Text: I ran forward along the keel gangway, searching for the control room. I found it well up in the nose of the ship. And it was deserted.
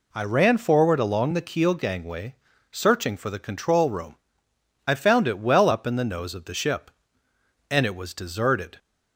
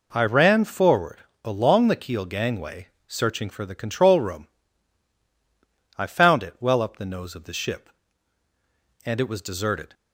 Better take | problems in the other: first | pauses between "forward" and "along"; slight; at 1.1 s; 0.24 s long // skips "in"; at 6.9 s

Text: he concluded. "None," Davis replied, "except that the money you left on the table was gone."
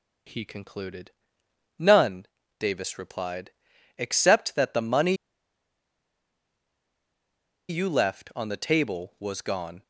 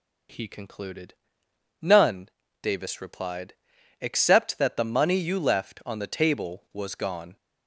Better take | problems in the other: second | pauses between "money" and "you"; strong; at 5.1 s; 2.5 s long

